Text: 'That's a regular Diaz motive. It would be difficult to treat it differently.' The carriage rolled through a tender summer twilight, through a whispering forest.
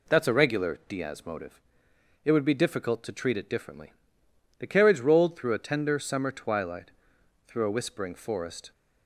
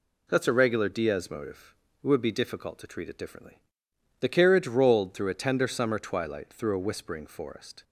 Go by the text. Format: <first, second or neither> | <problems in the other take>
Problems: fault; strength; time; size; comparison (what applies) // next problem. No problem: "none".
neither | none